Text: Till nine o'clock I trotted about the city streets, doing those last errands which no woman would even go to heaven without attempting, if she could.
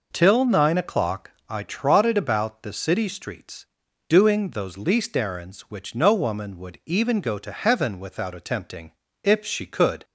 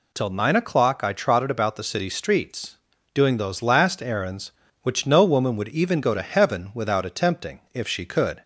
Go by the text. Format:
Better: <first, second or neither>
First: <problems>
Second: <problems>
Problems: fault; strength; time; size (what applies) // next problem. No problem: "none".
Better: second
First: pauses between "o'clock" and "I"; slight; at 1.2 s; 0.18 s long // says "least" for "last"; at 4.7 s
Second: none